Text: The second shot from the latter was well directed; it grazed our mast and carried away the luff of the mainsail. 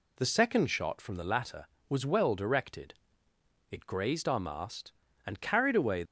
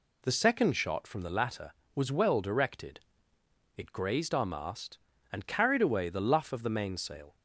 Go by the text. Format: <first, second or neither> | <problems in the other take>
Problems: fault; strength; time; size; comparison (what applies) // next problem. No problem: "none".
second | stops before "the luff of the mainsail"; at 6.0 s